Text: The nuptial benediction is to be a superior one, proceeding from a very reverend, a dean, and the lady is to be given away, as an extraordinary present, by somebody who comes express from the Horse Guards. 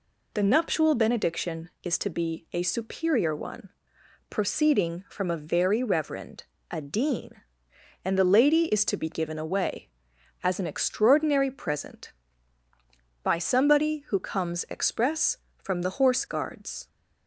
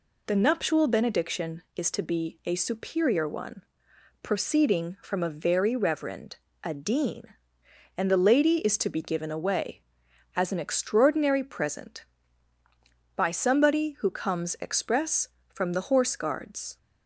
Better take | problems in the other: neither | none

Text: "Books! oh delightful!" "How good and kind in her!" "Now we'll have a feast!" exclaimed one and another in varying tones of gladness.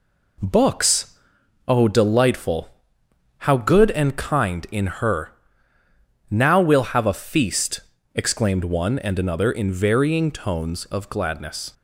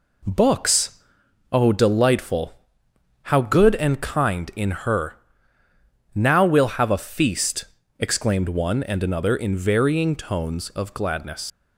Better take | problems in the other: first | leaves "gladness" unfinished; at 11.4 s; 75 ms

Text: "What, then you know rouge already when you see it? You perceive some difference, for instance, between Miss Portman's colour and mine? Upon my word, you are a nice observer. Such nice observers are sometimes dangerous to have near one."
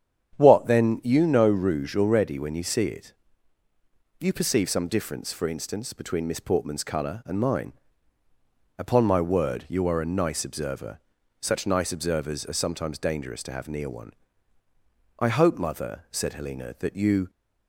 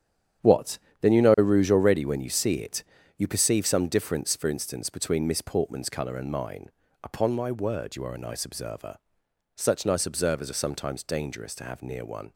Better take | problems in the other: second | starts louder than the rest; strong; until 1.4 s; 9 dB; strong in the second // goes on to say "I hope mother said Helena that you"; strong; from 15.1 s on; 2.1 s long

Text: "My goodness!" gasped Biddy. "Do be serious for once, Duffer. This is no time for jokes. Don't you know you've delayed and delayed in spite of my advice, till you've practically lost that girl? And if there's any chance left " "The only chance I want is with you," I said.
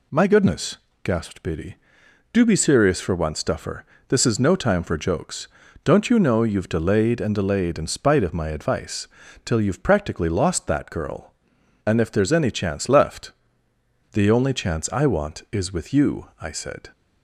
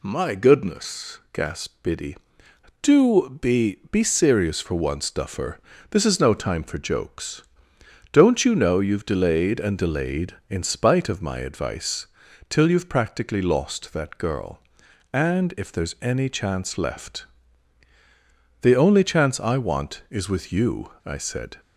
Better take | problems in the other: first | says "be" twice; at 3.9 s

